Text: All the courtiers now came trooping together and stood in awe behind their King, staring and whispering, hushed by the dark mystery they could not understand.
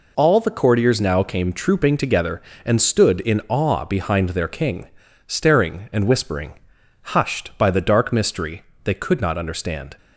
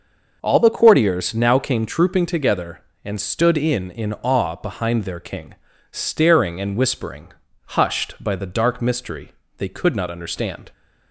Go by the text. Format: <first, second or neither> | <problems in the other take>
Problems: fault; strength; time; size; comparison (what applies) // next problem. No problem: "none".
first | says "in" twice; at 3.8 s // pauses between "mystery" and "they"; slight; at 9.3 s; 0.26 s long; slight in the first